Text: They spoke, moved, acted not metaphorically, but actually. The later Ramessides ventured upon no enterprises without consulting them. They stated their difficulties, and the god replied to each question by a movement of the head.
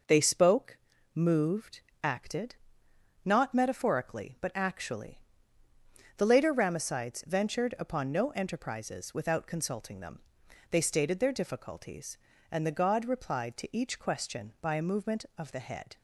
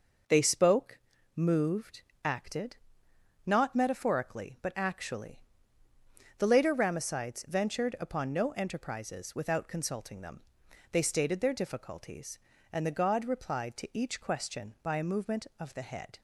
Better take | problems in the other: neither | pauses between "acted" and "not"; noticeable; the same in both

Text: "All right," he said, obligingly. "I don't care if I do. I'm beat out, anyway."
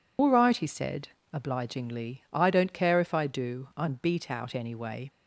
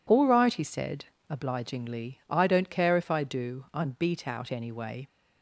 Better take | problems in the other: second | loses the start of "All"; at 0.1 s; 90 ms

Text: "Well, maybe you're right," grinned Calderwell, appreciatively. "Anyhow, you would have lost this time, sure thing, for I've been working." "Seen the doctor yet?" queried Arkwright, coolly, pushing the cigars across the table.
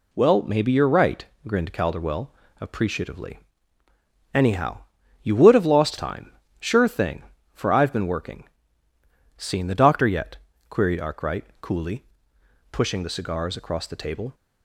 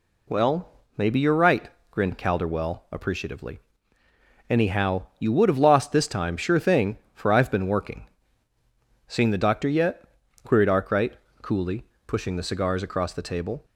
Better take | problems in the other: second | skips "this"; at 5.9 s

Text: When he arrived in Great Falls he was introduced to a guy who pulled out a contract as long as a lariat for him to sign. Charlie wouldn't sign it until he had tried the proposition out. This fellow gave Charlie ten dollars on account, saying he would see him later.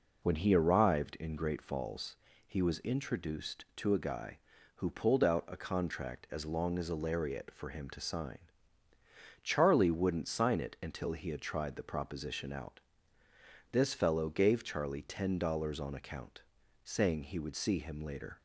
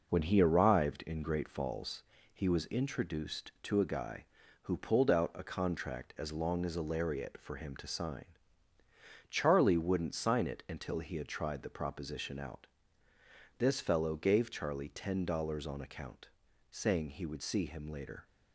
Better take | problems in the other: first | gets quieter; noticeable; throughout; 5 dB // pauses between "Falls" and "he"; slight; at 2.0 s; 0.32 s long; slight in the first

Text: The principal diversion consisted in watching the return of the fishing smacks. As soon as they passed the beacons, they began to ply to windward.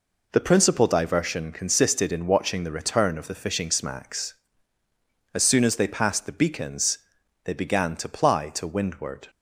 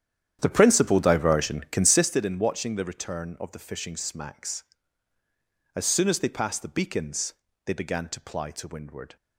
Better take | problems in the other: first | starts louder than the rest; strong; until 2.0 s; 9.5 dB

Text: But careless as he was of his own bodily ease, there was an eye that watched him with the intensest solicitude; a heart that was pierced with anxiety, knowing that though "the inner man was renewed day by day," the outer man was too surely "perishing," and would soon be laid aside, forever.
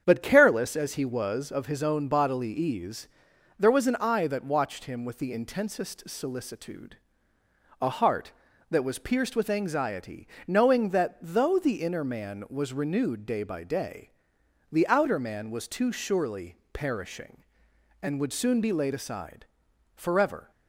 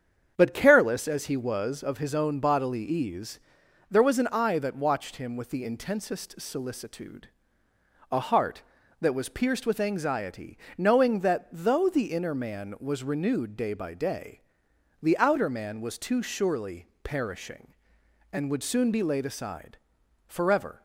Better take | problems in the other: neither | starts louder than the rest; strong; the same in both // pauses between "surely" and "perishing"; slight; the same in both

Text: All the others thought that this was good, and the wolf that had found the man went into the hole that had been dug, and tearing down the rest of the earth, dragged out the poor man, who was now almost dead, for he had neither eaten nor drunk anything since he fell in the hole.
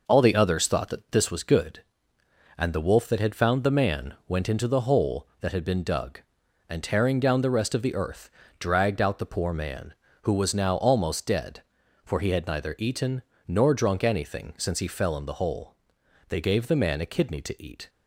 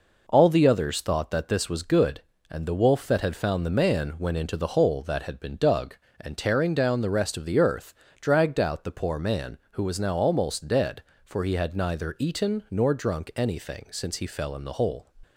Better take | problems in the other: second | pauses between "eaten" and "nor"; slight; at 13.2 s; 0.26 s long // goes on to say "They gave the man a kidney to eat"; from 16.2 s on; 1.6 s long

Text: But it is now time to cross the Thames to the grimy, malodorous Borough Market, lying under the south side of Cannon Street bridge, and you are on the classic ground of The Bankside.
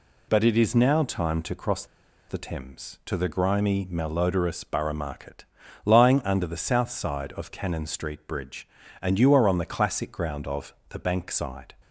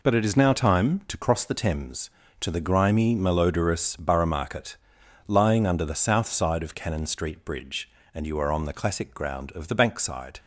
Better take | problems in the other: second | pauses between "cross" and "the"; at 1.8 s; 0.44 s long // pauses between "of" and "The"; slight; at 10.7 s; 0.16 s long

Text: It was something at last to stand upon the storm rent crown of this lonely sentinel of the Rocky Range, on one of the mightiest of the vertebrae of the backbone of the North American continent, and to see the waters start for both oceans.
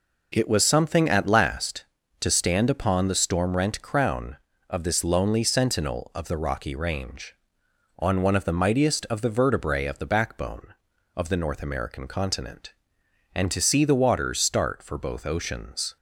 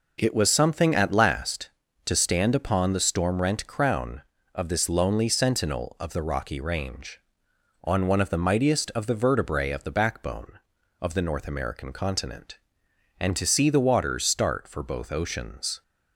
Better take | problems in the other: neither | none

